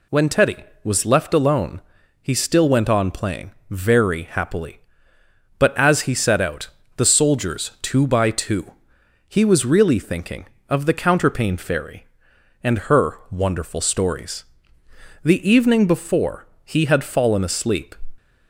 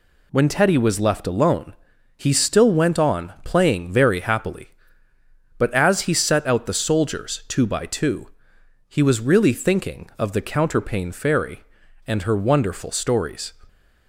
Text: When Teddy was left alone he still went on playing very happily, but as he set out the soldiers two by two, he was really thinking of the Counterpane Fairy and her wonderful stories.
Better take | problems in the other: second | pauses between "alone" and "he"; at 1.8 s; 0.40 s long; also in the second // pauses between "playing" and "very"; slight; at 3.5 s; 0.20 s long // pauses between "out" and "the"; slight; at 6.6 s; 0.30 s long // goes on to say "The evening before he had fallen asleep"; strong; from 15.2 s on; 2.7 s long

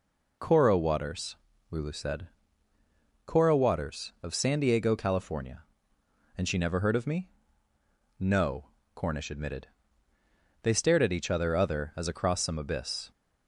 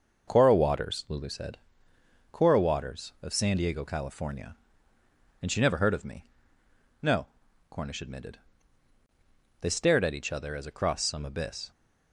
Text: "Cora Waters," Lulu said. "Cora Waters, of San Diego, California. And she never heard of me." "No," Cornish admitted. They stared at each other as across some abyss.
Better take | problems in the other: second | says "other" twice; at 11.5 s

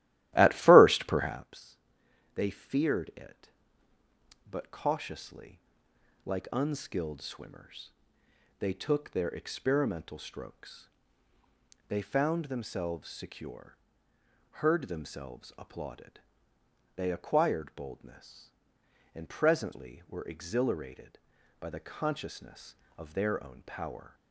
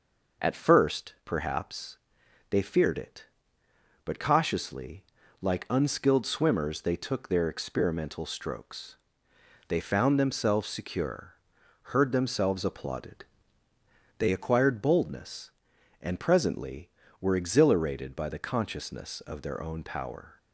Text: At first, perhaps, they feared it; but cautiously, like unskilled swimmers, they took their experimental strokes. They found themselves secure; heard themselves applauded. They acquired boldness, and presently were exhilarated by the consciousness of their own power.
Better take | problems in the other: second | starts louder than the rest; strong; until 1.5 s; 15 dB

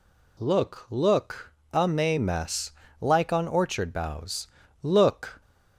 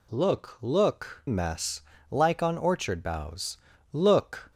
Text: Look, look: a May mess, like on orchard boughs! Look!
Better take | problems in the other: first | skips "a May"; at 1.2 s

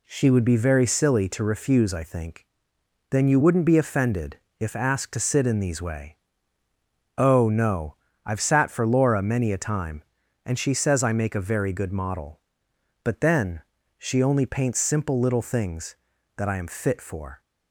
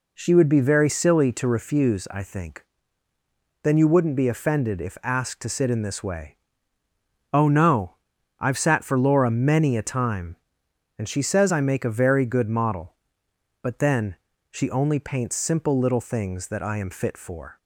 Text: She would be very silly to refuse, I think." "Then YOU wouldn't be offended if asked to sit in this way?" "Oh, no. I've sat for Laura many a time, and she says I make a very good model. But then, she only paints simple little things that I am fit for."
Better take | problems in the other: second | pauses between "offended" and "if"; slight; at 4.3 s; 0.20 s long // says "these" for "this"; at 5.6 s

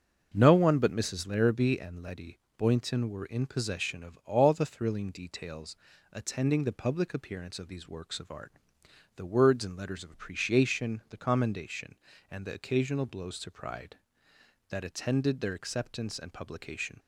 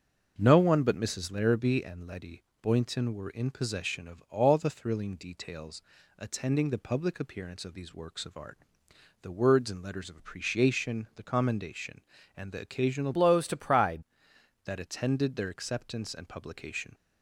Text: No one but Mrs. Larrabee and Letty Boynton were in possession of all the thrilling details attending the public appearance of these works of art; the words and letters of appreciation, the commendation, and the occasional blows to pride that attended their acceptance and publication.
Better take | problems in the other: first | starts louder than the rest; until 1.3 s; 6 dB; also in the first // pauses between "Letty" and "Boynton"; slight; at 2.4 s; 0.18 s long; slight in the first // pauses between "details" and "attending"; at 5.7 s; 0.38 s long; also in the first // changes voice from "blows" to "pride"; from 13.1 to 14.0 s; 0.9 s long

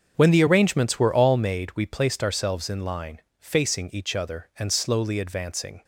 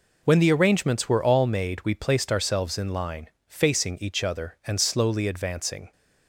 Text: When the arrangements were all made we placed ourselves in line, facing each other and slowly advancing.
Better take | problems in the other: second | starts louder than the rest; until 1.7 s; 7 dB

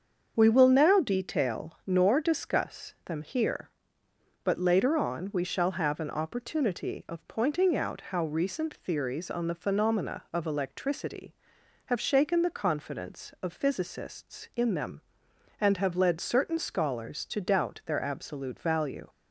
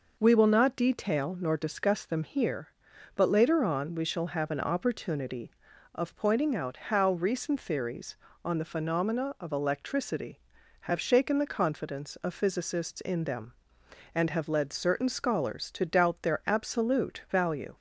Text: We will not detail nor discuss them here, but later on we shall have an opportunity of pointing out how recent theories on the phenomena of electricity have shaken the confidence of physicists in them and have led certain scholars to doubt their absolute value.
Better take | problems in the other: second | starts louder than the rest; until 1.3 s; 7 dB // says "now" for "not"; at 0.6 s

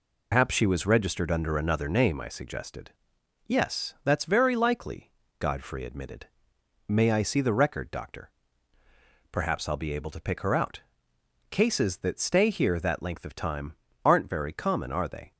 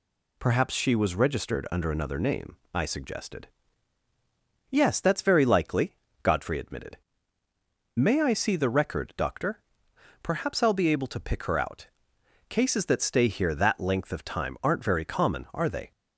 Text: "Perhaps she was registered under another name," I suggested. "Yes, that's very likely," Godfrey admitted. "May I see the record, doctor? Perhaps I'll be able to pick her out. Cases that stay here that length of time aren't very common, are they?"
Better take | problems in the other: second | loses the start of "Perhaps"; at 0.3 s; 145 ms // pauses between "time" and "aren't"; slight; at 13.7 s; 0.30 s long

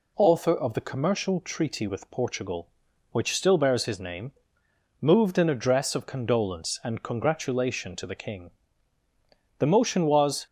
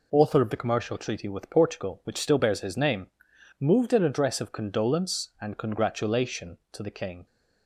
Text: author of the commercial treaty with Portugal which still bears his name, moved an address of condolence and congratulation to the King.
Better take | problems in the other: second | goes on to say "The motion was"; noticeable; from 9.5 s on; 0.88 s long

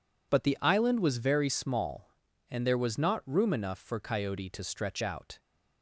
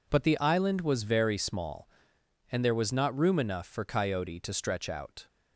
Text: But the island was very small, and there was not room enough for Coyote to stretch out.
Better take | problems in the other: neither | none

